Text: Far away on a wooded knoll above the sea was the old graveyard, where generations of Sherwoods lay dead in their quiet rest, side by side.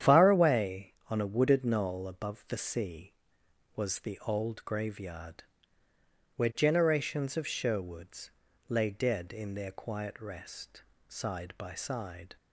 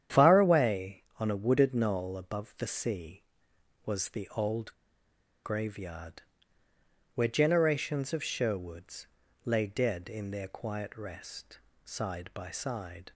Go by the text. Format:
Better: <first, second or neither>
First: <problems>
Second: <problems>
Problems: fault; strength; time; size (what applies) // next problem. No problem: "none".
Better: first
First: starts louder than the rest; strong; until 1.2 s; 9 dB // pauses between "Sherwoods" and "lay"; at 8.2 s; 0.38 s long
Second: starts louder than the rest; strong; until 1.3 s; 9.5 dB // pauses between "old" and "graveyard"; noticeable; at 4.7 s; 0.69 s long // pauses between "Sherwoods" and "lay"; at 9.0 s; 0.38 s long